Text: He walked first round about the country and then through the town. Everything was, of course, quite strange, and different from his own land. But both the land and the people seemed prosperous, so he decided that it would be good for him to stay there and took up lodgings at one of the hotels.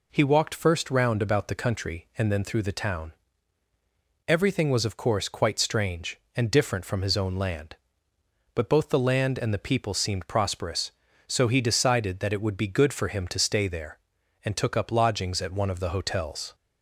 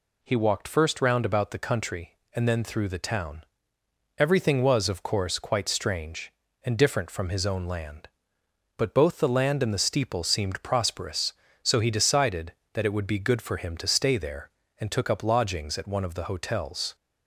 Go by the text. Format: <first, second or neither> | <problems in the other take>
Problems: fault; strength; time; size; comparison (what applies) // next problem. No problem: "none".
first | says "steeple" for "people"; at 9.7 s